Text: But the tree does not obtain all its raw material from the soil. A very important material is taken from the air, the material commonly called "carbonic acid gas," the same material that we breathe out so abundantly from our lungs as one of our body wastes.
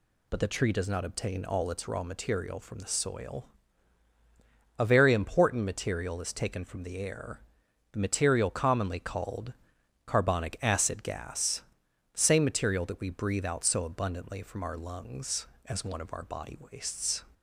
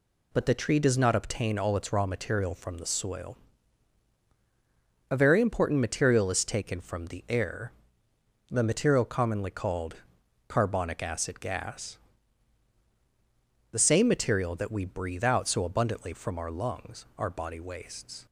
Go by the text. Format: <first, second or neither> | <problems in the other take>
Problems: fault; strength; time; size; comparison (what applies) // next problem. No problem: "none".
first | pauses between "called" and "carbonic"; noticeable; at 9.9 s; 0.52 s long; noticeable in the first // skips "as one of"; at 17.1 s